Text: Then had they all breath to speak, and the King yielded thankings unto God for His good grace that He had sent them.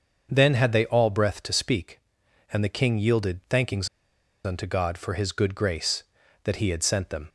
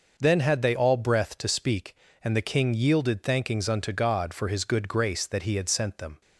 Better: second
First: starts louder than the rest; until 1.3 s; 6.5 dB // pauses between "thankings" and "unto"; noticeable; at 3.8 s; 0.58 s long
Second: none

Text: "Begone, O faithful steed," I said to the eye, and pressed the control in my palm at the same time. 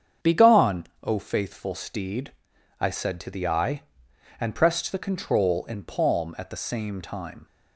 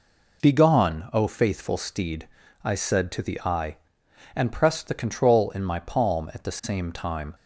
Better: second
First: starts louder than the rest; strong; until 1.3 s; 7.5 dB // skips "my"; at 5.8 s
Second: none

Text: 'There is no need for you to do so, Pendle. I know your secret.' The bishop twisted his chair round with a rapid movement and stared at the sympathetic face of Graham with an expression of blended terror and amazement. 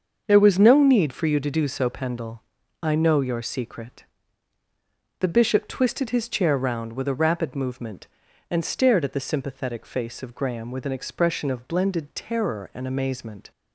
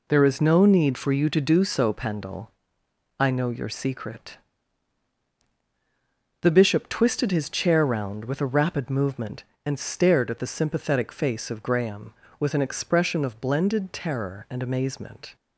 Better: second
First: starts louder than the rest; until 1.2 s; 6.5 dB // says "was" for "is"; at 0.3 s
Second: none

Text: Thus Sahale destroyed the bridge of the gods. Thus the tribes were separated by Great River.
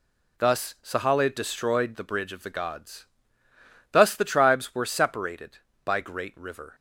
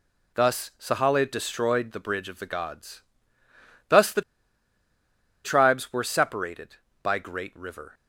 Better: first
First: none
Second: pauses between "the" and "tribes"; at 4.2 s; 1.2 s long

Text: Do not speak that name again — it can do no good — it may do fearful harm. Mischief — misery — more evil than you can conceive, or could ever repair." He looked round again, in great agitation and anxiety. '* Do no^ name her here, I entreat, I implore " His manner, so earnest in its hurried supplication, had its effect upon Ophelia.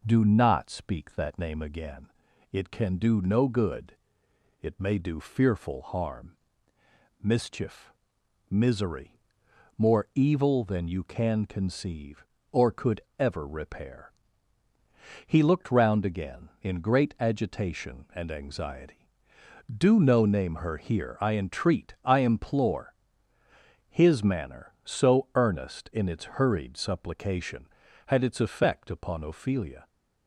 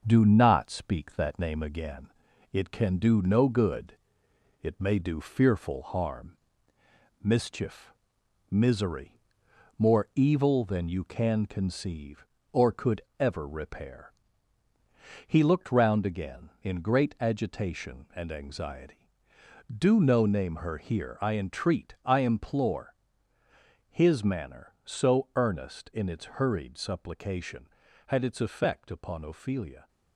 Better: first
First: pauses between "could" and "ever"; slight; at 12.9 s; 0.18 s long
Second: gets quieter; noticeable; throughout; 5.5 dB // pauses between "could" and "ever"; slight; at 12.9 s; 0.18 s long

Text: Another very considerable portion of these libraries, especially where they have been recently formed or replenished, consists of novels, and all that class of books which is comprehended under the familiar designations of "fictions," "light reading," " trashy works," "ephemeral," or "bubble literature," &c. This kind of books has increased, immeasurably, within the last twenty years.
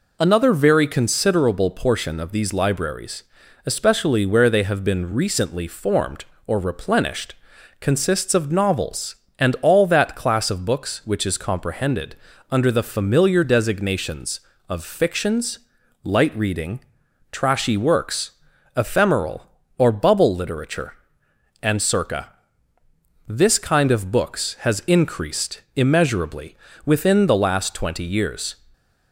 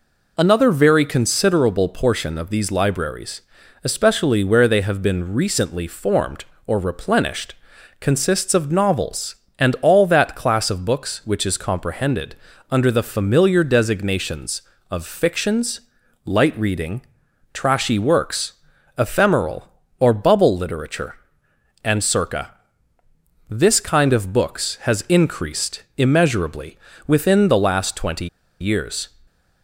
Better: first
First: pauses between "comprehended" and "under"; slight; at 12.1 s; 0.36 s long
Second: pauses between "comprehended" and "under"; slight; at 12.3 s; 0.36 s long // pauses between "twenty" and "years"; slight; at 28.2 s; 0.32 s long

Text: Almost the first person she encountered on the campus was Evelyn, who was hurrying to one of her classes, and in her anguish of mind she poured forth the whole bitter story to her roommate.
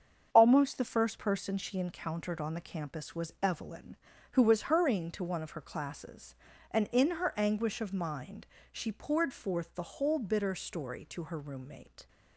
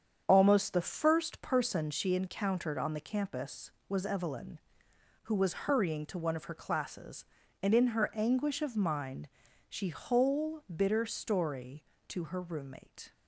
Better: first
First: starts louder than the rest; strong; until 1.3 s; 7 dB // pauses between "mind" and "she"; slight; at 8.4 s; 0.26 s long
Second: starts louder than the rest; strong; until 1.2 s; 8 dB // pauses between "mind" and "she"; at 9.2 s; 0.40 s long // skips "poured forth the"; at 9.8 s

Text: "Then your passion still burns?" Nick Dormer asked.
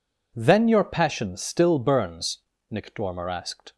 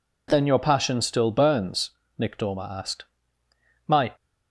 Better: first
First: none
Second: goes on to say "My"; slight; from 3.8 s on; 0.26 s long

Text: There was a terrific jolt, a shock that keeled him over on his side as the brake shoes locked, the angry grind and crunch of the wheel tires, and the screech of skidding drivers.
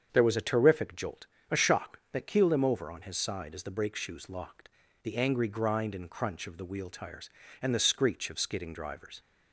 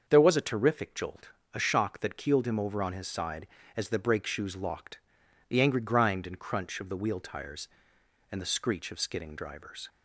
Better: neither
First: starts louder than the rest; strong; until 1.1 s; 7.5 dB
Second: starts louder than the rest; until 1.0 s; 6.5 dB

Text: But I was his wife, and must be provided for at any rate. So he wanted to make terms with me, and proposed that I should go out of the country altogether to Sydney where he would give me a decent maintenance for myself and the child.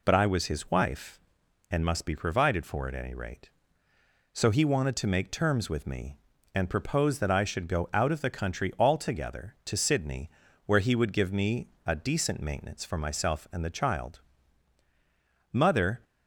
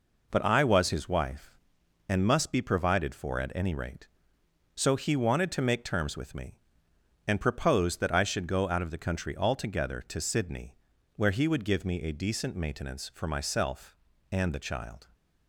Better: second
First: pauses between "Sydney" and "where"; slight; at 10.2 s; 0.36 s long // pauses between "me" and "a"; slight; at 11.6 s; 0.18 s long // goes on to say "Mother"; from 15.5 s on; 0.52 s long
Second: pauses between "Sydney" and "where"; at 10.7 s; 0.40 s long

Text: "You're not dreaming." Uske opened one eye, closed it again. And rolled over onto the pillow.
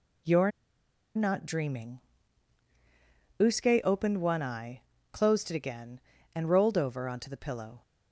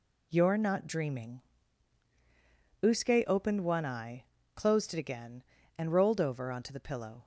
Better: second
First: pauses between "You're" and "not"; noticeable; at 0.5 s; 0.67 s long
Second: none

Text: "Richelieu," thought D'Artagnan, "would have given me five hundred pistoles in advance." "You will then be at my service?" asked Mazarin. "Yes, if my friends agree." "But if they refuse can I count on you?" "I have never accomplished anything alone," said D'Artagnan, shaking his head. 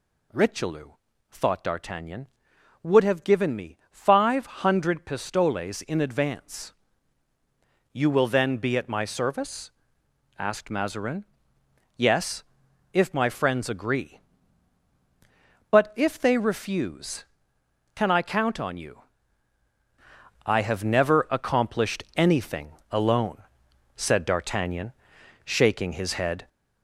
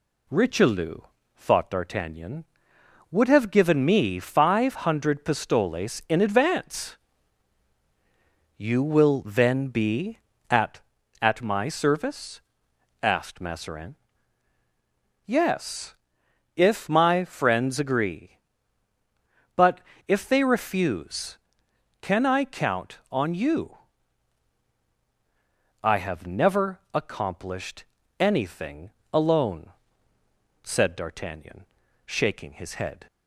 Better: first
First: pauses between "anything" and "alone"; slight; at 22.7 s; 0.18 s long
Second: says "at" twice; at 11.2 s // pauses between "But" and "if"; slight; at 19.7 s; 0.28 s long // pauses between "accomplished" and "anything"; slight; at 27.8 s; 0.34 s long // pauses between "anything" and "alone"; slight; at 28.9 s; 0.20 s long

